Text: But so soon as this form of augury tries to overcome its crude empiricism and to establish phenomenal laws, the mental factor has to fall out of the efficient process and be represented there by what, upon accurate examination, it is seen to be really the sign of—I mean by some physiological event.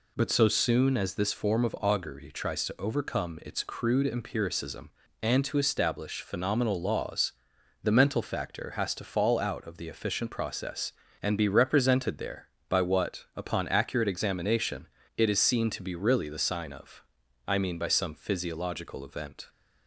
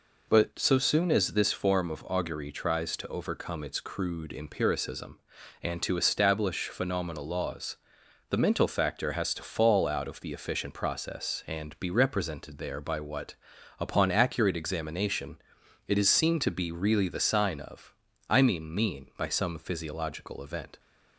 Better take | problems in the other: first | says "mean" twice; at 18.7 s

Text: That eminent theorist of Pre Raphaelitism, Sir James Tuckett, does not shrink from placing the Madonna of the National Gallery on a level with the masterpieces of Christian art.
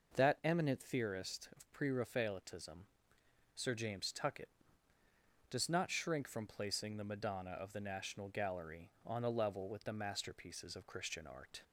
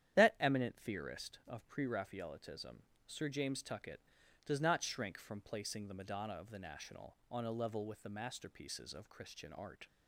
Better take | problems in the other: first | starts louder than the rest; strong; until 1.2 s; 10 dB // skips "Gallery"; at 7.2 s

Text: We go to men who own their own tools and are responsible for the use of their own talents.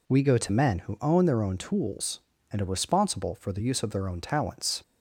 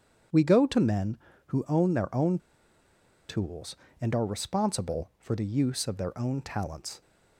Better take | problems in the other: first | starts louder than the rest; strong; until 1.6 s; 8 dB // pauses between "own" and "tools"; noticeable; at 2.3 s; 0.90 s long

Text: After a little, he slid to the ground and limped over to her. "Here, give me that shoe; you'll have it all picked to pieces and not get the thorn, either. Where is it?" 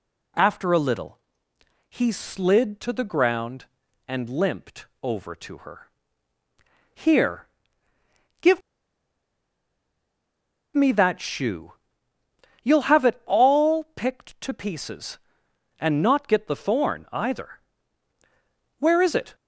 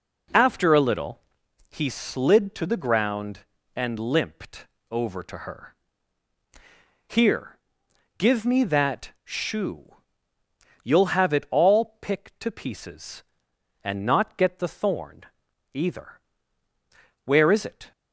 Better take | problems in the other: second | pauses between "limped" and "over"; slight; at 4.8 s; 0.16 s long; slight in the second // pauses between "give" and "me"; strong; at 8.5 s; 2.1 s long

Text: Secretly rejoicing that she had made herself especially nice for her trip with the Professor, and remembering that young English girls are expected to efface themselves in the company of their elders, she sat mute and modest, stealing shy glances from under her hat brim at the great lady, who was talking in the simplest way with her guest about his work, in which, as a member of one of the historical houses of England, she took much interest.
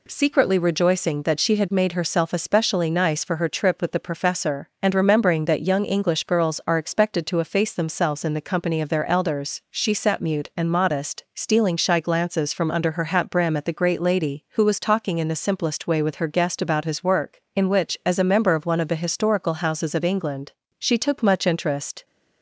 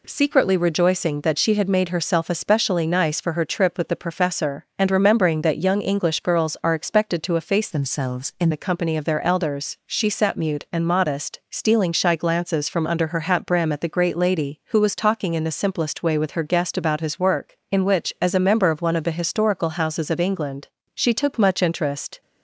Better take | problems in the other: first | changes voice from "themselves" to "in"; from 7.6 to 8.4 s; 0.8 s long

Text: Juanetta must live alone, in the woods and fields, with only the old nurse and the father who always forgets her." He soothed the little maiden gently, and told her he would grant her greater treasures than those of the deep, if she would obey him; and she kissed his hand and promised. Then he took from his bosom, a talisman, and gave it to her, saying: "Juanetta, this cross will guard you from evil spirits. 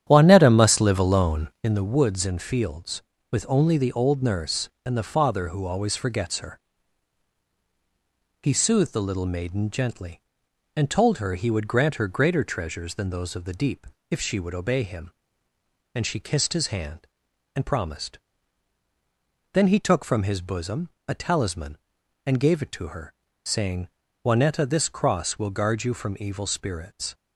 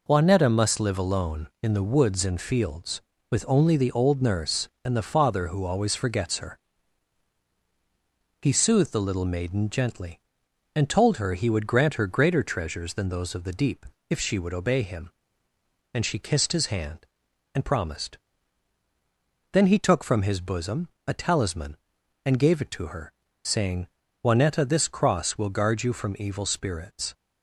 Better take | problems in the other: second | starts louder than the rest; strong; until 1.8 s; 10 dB

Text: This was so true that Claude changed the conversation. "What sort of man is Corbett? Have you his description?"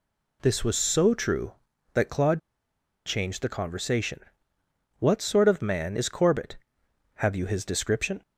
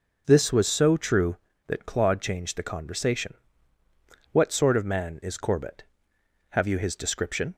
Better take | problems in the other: second | pauses between "Claude" and "changed"; noticeable; at 2.3 s; 0.65 s long

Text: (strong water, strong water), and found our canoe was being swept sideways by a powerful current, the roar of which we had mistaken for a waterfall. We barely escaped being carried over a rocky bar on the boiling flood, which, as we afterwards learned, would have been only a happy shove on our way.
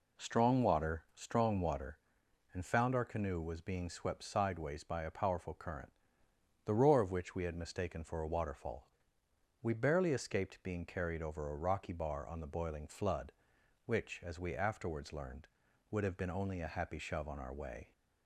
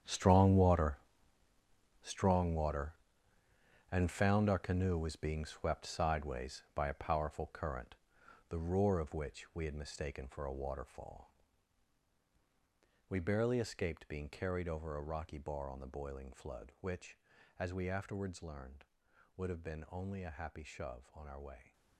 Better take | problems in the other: first | gets quieter; strong; throughout; 14 dB

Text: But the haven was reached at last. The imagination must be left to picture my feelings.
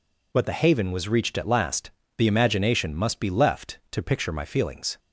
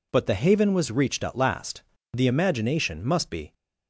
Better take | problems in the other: first | stops before "left to picture my feelings"; at 3.5 s

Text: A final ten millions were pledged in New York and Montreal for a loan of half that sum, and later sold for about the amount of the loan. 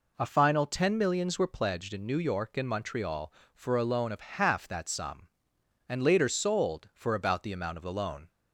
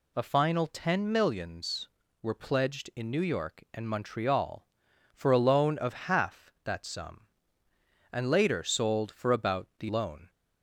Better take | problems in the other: first | skips "amount of the"; at 9.8 s

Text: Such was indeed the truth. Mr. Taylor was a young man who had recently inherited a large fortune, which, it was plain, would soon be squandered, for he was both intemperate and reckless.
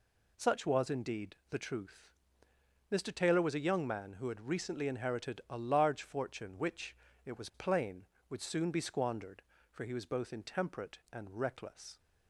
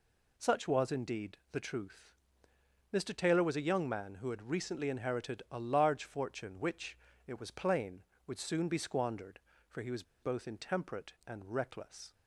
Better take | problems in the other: first | pauses between "was" and "both"; slight; at 10.0 s; 0.19 s long

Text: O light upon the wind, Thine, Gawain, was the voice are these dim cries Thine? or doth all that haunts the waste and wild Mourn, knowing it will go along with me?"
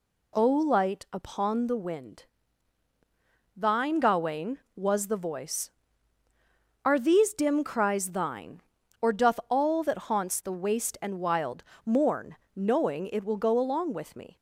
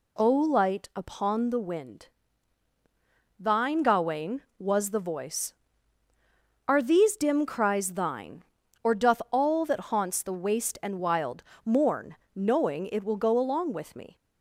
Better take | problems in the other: neither | pauses between "wild" and "Mourn"; slight; the same in both

